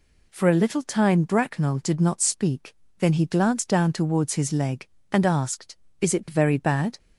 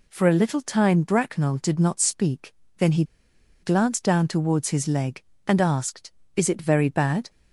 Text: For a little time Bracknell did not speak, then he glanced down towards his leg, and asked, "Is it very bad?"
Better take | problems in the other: first | pauses between "he" and "glanced"; noticeable; at 3.0 s; 0.59 s long

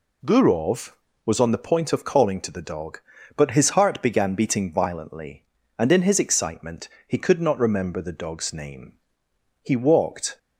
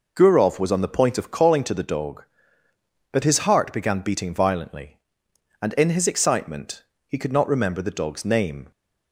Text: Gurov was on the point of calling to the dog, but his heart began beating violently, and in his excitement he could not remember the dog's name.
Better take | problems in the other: second | pauses between "excitement" and "he"; slight; at 6.8 s; 0.18 s long; slight in the second // goes on to say "He walked"; noticeable; from 9.6 s on; 0.76 s long

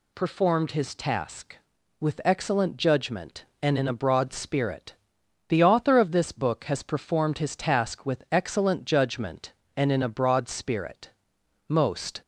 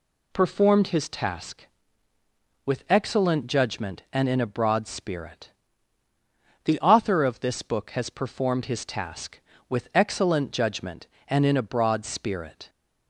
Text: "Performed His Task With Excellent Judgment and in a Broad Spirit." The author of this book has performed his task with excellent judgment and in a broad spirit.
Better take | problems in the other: second | goes on to say "Most"; from 11.6 s on; 0.54 s long

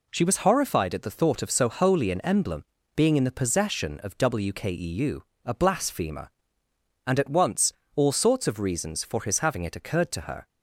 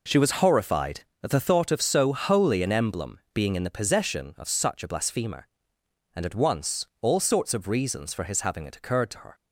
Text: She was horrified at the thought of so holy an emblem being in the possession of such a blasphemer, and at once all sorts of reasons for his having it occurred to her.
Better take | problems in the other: second | pauses between "emblem" and "being"; slight; at 2.6 s; 0.30 s long // says "wkeu" for "such"; at 4.1 s // pauses between "once" and "all"; slight; at 7.7 s; 0.22 s long

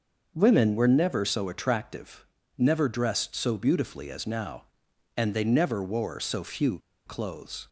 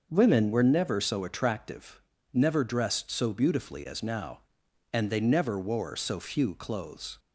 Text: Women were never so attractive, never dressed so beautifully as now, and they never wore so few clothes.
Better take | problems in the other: second | starts louder than the rest; noticeable; until 1.3 s; 6 dB; noticeable in the second // pauses between "few" and "clothes"; slight; at 6.7 s; 0.27 s long

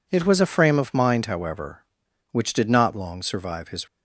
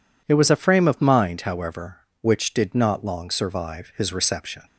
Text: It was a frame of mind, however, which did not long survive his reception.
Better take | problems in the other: second | stops before "reception"; at 3.8 s

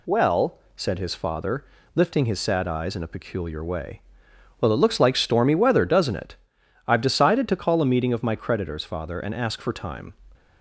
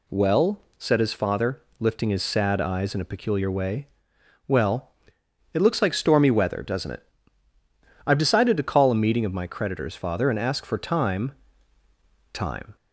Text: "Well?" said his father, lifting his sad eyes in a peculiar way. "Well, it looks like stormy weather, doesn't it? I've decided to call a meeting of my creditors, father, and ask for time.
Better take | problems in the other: first | says "time" twice; at 12.3 s

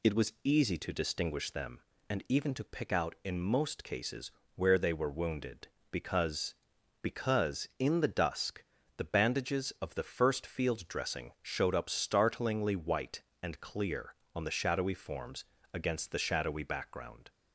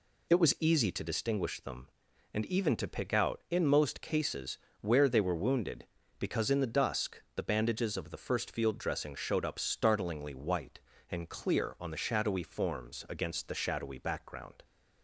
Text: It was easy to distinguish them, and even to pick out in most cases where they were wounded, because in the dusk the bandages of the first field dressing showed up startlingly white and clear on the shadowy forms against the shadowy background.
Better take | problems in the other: second | pauses between "cases" and "where"; slight; at 4.3 s; 0.24 s long; slight in the second // says "because" twice; at 7.0 s // pauses between "dusk" and "the"; slight; at 8.6 s; 0.32 s long // pauses between "forms" and "against"; slight; at 15.4 s; 0.28 s long

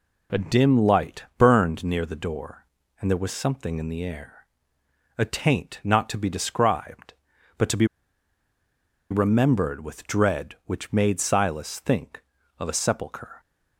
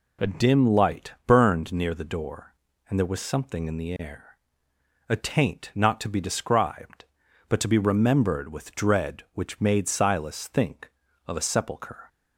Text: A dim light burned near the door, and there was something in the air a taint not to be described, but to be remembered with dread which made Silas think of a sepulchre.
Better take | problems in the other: second | pauses between "air" and "a"; noticeable; at 4.4 s; 0.72 s long; noticeable in the second // pauses between "be" and "remembered"; strong; at 7.8 s; 1.2 s long

